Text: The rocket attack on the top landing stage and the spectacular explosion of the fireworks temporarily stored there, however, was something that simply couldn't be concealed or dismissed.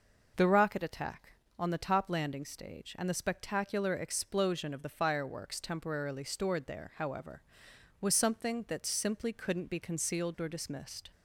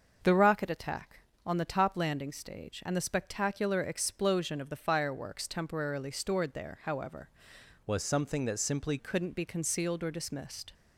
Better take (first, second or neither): first